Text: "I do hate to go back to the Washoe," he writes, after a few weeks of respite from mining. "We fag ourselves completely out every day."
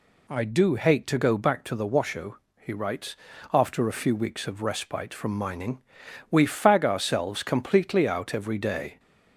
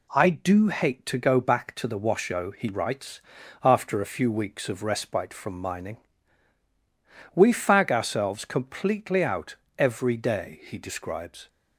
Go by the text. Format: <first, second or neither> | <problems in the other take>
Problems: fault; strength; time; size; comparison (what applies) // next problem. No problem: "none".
first | pauses between "out" and "every"; slight; at 9.5 s; 0.20 s long // goes on to say "He describes"; noticeable; from 10.6 s on; 0.84 s long